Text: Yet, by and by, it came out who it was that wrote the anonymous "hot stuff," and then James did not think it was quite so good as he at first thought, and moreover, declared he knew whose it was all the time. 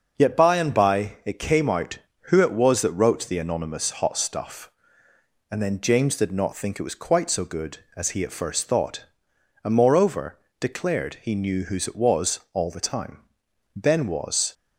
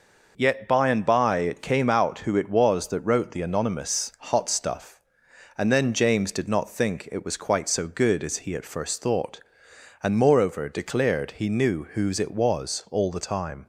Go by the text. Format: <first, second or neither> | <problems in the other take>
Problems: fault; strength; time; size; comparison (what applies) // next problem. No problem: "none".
second | goes on to say "Ben was"; noticeable; from 13.7 s on; 0.78 s long